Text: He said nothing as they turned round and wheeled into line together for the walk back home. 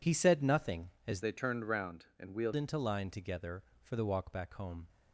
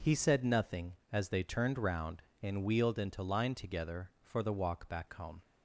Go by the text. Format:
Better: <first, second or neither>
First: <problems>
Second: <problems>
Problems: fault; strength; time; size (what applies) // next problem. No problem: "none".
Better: second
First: changes voice from "they" to "wheeled"; from 1.2 to 2.5 s; 1.3 s long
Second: none